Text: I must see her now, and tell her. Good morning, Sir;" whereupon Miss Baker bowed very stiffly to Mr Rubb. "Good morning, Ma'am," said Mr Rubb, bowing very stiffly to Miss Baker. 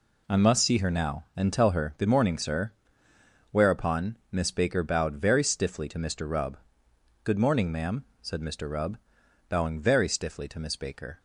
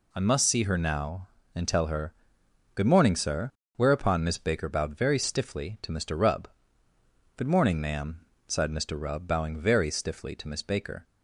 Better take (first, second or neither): first